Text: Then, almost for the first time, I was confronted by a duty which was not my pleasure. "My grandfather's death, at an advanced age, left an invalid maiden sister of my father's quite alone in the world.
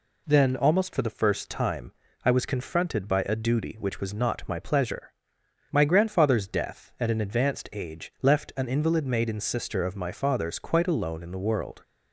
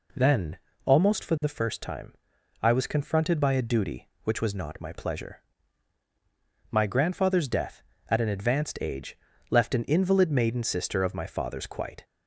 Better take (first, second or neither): first